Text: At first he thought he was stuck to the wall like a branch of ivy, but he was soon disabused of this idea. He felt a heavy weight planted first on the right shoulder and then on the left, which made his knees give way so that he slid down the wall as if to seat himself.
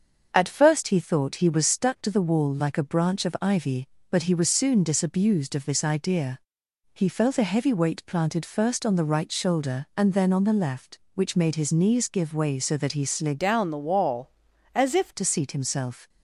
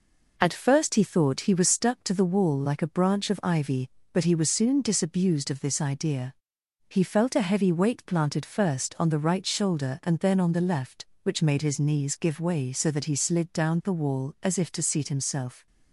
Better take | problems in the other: second | starts louder than the rest; until 1.3 s; 7 dB // changes voice from "down" to "if"; from 13.3 to 15.1 s; 1.8 s long

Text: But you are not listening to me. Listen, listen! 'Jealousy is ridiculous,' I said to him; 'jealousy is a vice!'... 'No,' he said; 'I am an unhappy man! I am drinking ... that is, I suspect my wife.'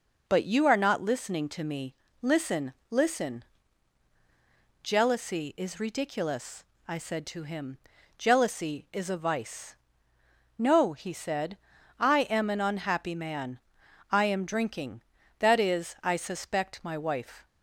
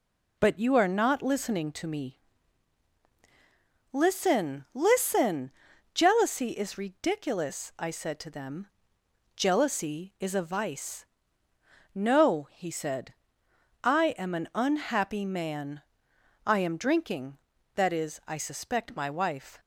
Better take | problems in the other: first | says "them" for "him"; at 8.2 s

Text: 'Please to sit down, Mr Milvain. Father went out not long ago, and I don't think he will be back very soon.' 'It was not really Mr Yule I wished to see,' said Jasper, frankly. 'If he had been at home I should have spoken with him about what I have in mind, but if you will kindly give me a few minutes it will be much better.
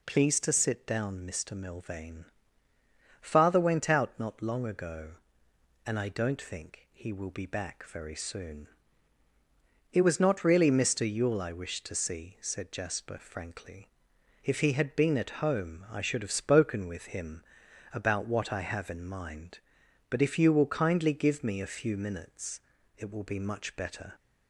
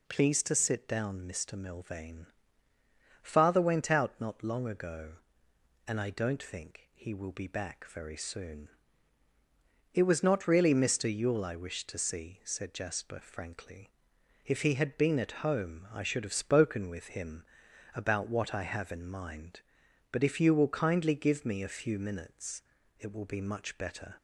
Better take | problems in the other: neither | pauses between "him" and "about"; noticeable; the same in both // pauses between "minutes" and "it"; the same in both

